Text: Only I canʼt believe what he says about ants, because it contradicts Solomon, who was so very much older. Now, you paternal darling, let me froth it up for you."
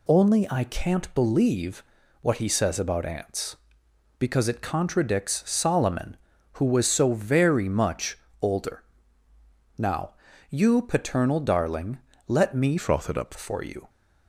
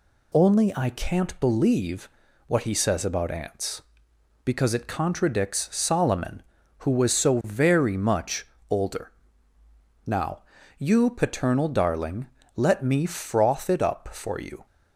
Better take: second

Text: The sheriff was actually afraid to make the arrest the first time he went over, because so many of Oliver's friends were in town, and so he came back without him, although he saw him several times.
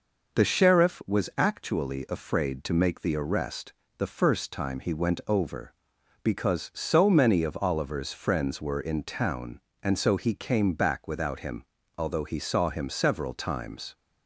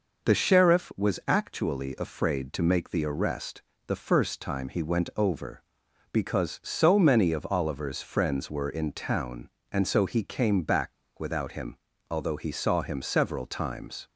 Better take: first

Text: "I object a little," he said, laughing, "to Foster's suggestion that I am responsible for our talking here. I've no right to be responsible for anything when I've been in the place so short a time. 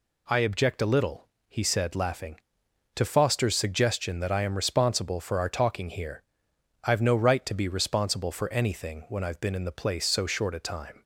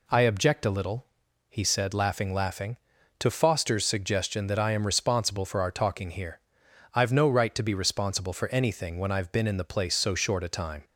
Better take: first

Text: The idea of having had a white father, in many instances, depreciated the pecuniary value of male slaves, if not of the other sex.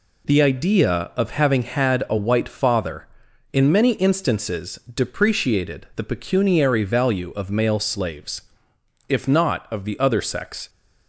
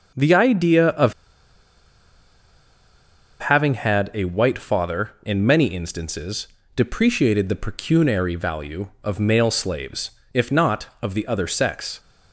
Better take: first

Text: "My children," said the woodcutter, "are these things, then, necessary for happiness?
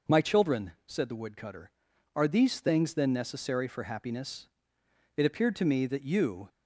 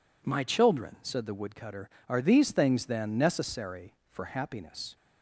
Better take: second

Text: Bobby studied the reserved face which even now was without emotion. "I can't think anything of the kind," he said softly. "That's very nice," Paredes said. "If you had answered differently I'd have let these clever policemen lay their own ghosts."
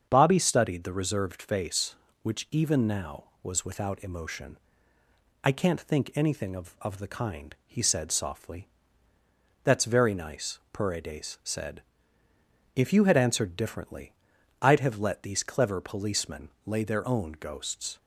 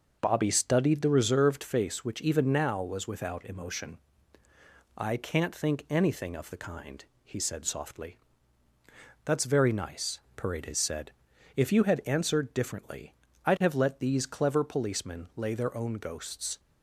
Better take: second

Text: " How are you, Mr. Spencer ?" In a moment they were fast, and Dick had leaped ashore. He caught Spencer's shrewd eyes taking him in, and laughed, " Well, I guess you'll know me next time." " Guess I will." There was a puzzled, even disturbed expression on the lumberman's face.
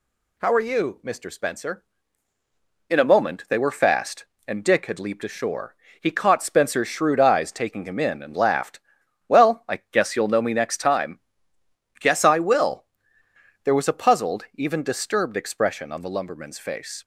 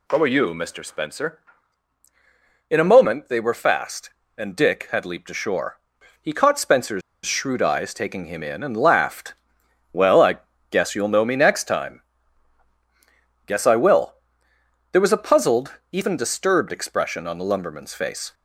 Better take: first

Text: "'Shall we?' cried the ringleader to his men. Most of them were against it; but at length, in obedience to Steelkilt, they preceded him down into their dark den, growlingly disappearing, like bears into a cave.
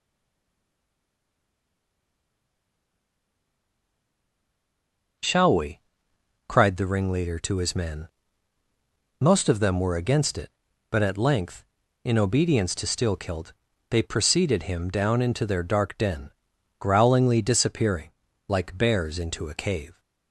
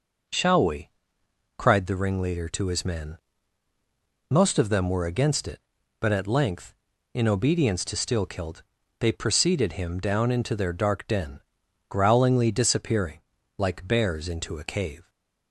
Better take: second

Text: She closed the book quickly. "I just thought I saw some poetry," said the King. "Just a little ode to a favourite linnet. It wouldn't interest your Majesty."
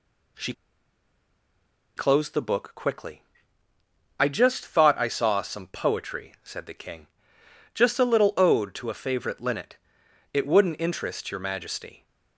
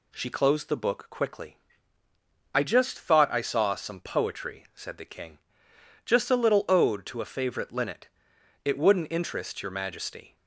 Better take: second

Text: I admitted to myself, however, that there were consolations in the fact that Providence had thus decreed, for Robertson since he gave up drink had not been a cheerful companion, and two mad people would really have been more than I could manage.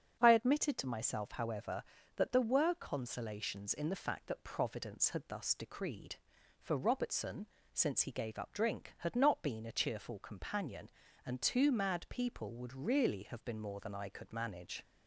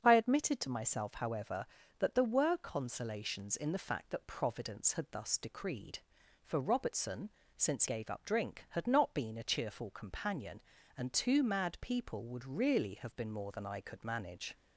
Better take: first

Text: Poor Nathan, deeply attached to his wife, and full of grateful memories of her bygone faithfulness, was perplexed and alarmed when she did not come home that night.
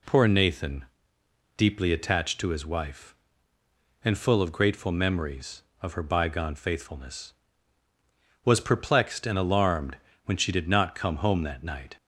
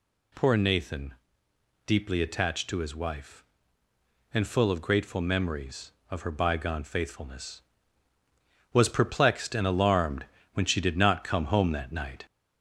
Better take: first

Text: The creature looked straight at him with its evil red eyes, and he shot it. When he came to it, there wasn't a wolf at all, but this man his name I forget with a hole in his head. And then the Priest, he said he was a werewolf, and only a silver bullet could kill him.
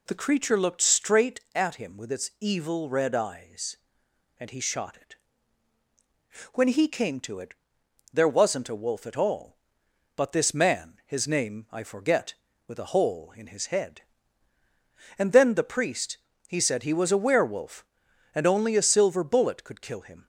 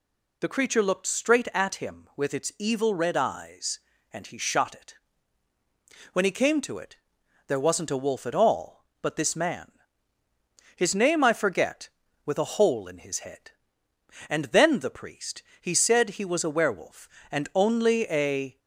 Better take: first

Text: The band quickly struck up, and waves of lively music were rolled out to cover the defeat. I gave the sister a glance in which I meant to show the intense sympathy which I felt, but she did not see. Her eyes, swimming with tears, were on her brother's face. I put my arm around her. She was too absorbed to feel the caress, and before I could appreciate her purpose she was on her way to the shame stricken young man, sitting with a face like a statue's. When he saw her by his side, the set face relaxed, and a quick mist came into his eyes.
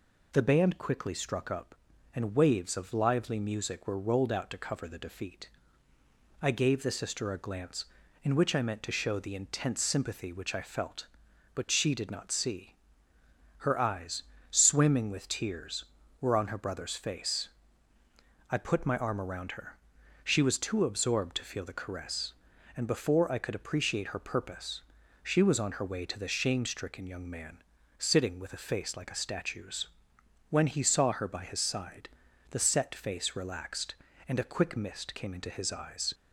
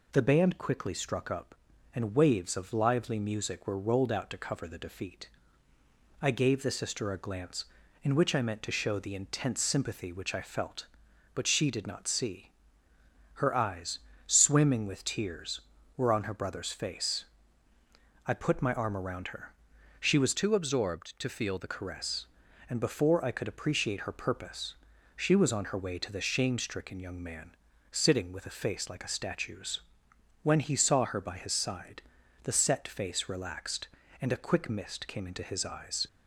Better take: first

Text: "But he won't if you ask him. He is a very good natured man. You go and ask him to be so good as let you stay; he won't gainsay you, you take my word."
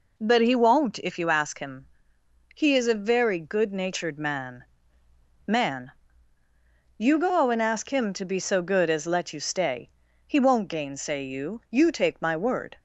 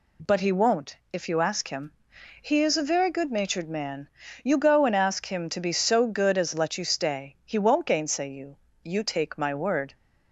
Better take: second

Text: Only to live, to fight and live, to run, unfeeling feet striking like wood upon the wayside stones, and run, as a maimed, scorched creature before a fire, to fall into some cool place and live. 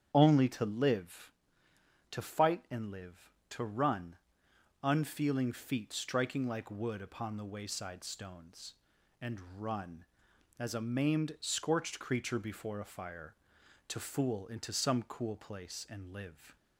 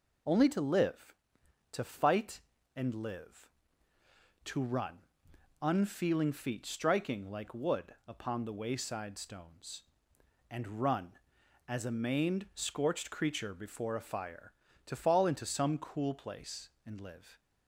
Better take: second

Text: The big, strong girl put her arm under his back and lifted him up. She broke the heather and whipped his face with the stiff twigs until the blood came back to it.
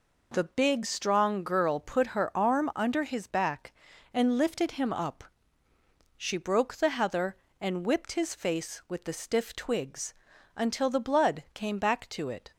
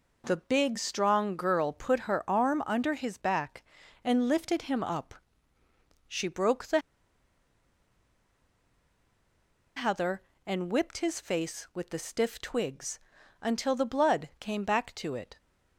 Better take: first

